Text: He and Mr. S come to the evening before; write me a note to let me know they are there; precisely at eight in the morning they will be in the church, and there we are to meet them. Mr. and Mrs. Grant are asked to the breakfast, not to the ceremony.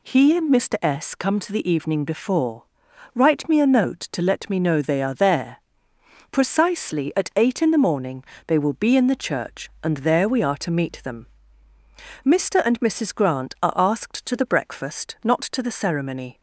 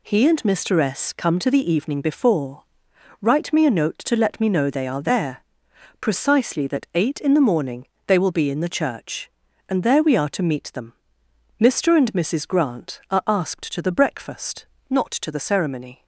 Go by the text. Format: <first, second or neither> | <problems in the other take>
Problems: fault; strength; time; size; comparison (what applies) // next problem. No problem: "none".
first | says "that" for "at"; at 6.6 s // pauses between "morning" and "they"; slight; at 7.8 s; 0.22 s long; slight in the first